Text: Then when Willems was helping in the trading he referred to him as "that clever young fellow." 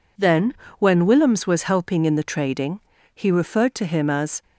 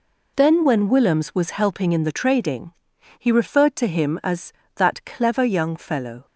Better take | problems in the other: second | pauses between "Then" and "when"; slight; at 0.5 s; 0.24 s long // pauses between "trading" and "he"; at 2.7 s; 0.38 s long; noticeable in the second // stops before "that clever young fellow"; at 4.4 s

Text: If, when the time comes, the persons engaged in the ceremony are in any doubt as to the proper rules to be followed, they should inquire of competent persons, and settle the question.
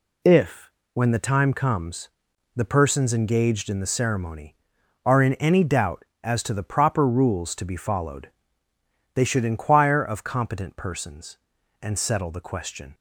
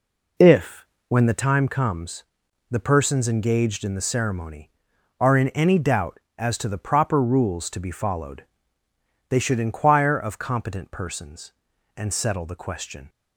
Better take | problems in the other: first | starts louder than the rest; until 1.5 s; 3.5 dB

